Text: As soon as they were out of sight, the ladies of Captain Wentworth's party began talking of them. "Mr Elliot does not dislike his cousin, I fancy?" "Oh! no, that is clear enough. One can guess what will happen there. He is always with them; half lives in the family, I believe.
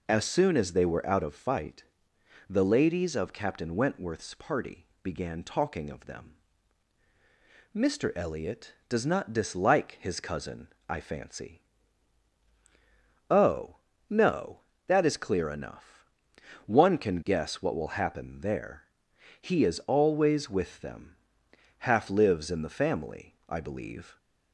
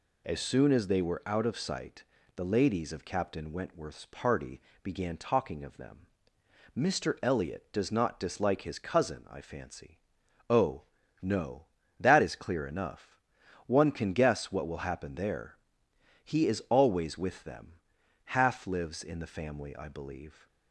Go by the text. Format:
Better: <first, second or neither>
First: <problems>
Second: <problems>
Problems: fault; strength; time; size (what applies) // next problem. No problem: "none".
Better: second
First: says "fight" for "sight"; at 1.3 s // pauses between "party" and "began"; slight; at 4.8 s; 0.16 s long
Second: pauses between "party" and "began"; slight; at 4.5 s; 0.22 s long